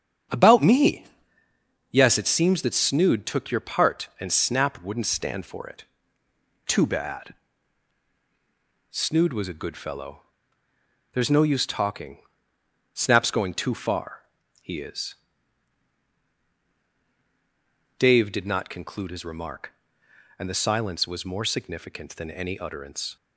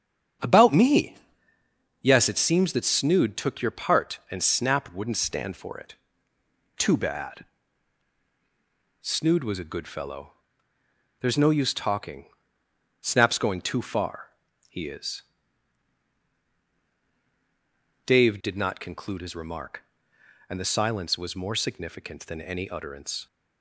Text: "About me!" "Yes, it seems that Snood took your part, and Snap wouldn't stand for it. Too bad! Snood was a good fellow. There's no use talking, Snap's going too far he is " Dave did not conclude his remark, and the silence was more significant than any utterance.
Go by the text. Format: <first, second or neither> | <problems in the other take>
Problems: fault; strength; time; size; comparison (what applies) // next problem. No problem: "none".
neither | starts louder than the rest; strong; the same in both // pauses between "far" and "he"; the same in both